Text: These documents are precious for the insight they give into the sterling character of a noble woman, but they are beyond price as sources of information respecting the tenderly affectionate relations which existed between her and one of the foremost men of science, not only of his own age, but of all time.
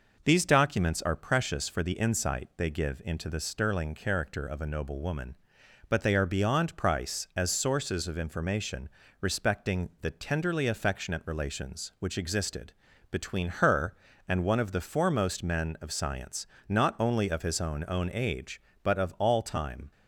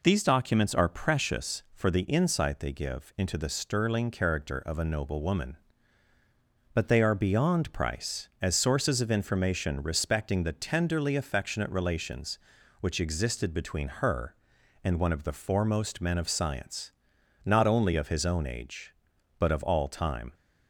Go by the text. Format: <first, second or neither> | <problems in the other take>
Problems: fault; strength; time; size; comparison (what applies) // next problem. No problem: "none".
second | pauses between "information" and "respecting"; slight; at 8.8 s; 0.32 s long // pauses between "existed" and "between"; at 12.7 s; 0.38 s long // says "own" twice; at 17.8 s